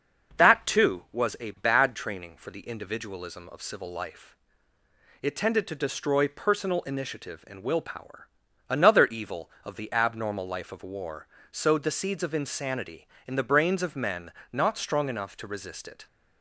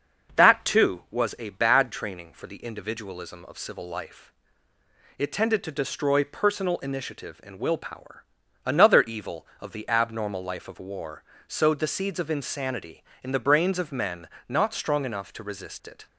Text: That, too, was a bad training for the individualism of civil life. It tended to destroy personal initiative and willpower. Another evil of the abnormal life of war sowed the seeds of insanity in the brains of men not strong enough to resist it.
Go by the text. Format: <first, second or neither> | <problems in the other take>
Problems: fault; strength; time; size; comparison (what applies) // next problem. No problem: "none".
neither | starts louder than the rest; the same in both // pauses between "war" and "sowed"; slight; the same in both // pauses between "men" and "not"; slight; the same in both